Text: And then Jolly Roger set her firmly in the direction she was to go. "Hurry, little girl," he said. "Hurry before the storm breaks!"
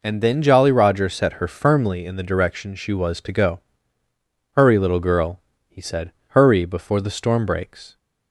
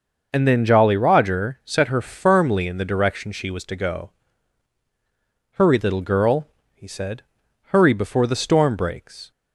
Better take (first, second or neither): neither